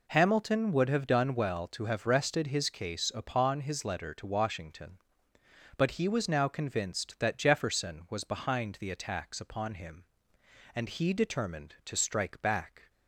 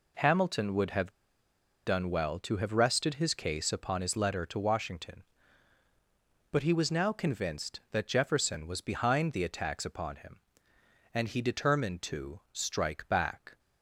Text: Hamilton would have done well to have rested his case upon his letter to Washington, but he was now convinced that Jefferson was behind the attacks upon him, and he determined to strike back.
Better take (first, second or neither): first